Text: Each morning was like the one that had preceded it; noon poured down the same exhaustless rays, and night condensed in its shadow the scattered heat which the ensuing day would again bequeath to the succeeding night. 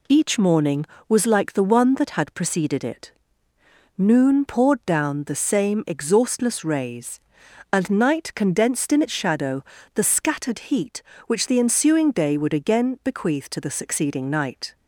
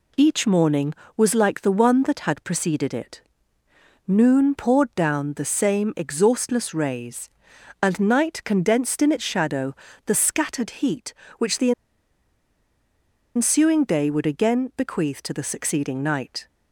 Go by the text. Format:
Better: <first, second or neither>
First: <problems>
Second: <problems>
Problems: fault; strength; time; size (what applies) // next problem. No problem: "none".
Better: first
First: pauses between "shadow" and "the"; slight; at 9.6 s; 0.32 s long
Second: pauses between "shadow" and "the"; slight; at 9.7 s; 0.32 s long // pauses between "the" and "ensuing"; strong; at 11.7 s; 1.6 s long